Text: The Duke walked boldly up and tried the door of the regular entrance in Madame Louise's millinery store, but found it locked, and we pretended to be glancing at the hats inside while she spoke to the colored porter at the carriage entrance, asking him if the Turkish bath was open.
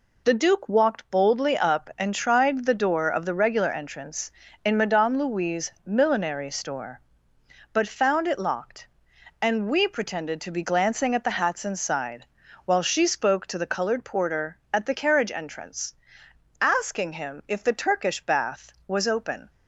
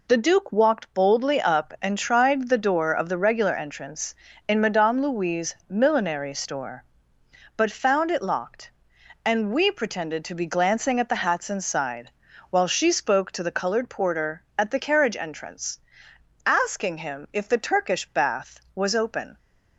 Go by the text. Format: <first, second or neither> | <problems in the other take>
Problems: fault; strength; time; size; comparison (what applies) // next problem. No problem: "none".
neither | pauses between "inside" and "while"; the same in both